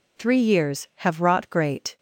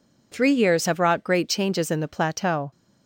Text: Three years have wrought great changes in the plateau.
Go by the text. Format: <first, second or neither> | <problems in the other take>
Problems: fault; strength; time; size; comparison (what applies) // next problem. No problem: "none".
second | stops before "changes in the plateau"; at 1.9 s